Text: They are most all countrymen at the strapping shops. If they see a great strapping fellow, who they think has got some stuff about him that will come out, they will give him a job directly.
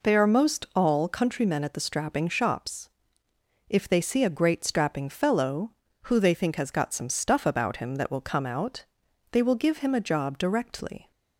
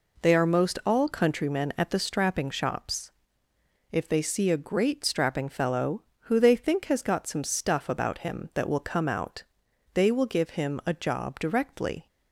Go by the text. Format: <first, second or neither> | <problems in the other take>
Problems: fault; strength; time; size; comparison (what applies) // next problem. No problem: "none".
neither | none